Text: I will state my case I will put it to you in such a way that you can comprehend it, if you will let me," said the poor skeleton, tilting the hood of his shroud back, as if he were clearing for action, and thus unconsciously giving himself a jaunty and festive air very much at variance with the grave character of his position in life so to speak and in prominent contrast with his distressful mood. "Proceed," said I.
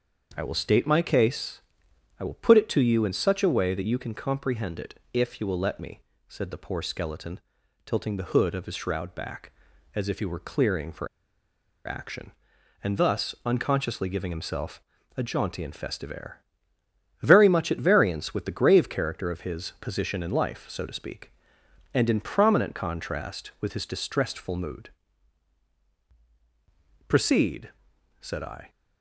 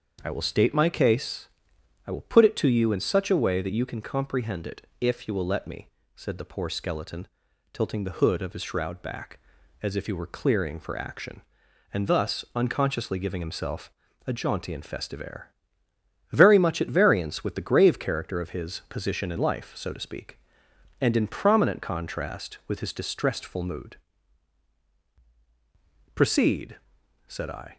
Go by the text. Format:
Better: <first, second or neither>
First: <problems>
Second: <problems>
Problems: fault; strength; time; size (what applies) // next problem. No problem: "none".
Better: second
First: starts louder than the rest; until 1.3 s; 6.5 dB // pauses between "case" and "I"; noticeable; at 1.6 s; 0.60 s long // pauses between "for" and "action"; noticeable; at 11.0 s; 0.79 s long // pauses between "himself" and "a"; slight; at 14.8 s; 0.34 s long // pauses between "air" and "very"; noticeable; at 16.4 s; 0.80 s long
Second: starts louder than the rest; until 1.2 s; 6.5 dB // pauses between "case" and "I"; noticeable; at 1.4 s; 0.60 s long // pauses between "himself" and "a"; slight; at 13.9 s; 0.34 s long // pauses between "air" and "very"; noticeable; at 15.5 s; 0.80 s long